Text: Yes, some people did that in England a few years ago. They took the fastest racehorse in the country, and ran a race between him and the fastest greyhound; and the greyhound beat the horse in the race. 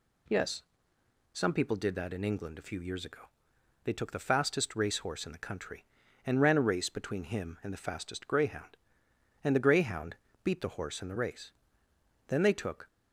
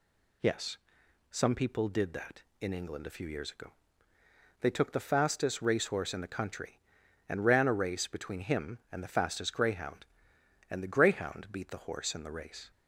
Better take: second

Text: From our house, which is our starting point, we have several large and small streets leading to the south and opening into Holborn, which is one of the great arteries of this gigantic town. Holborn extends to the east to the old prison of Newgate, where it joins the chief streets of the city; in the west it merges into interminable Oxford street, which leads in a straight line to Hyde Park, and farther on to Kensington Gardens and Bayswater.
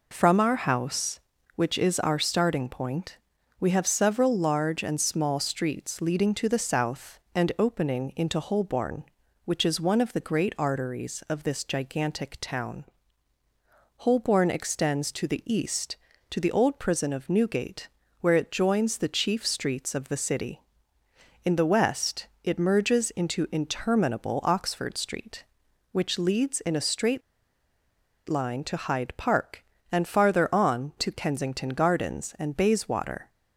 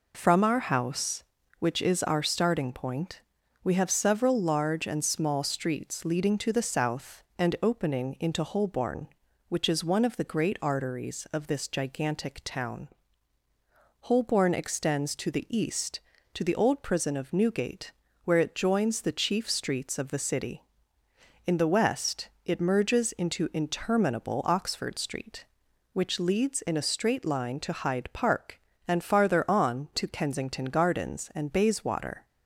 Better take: second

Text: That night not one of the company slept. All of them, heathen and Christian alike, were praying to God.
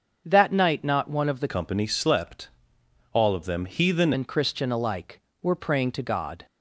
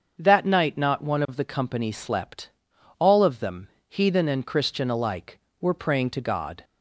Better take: second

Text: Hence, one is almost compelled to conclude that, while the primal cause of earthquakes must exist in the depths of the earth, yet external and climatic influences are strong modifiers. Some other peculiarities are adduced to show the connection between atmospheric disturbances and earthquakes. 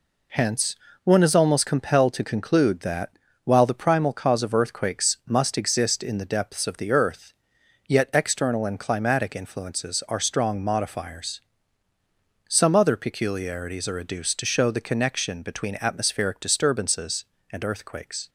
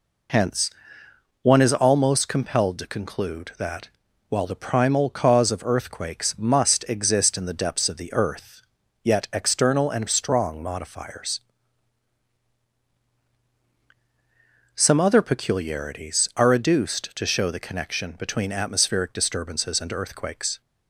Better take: first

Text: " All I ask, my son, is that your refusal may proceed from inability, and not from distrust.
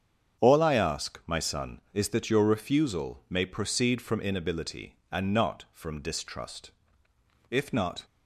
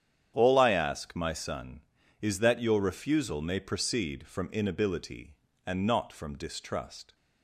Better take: second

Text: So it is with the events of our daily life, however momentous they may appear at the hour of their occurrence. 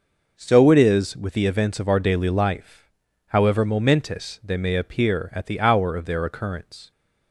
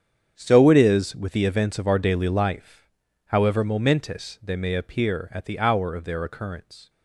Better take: first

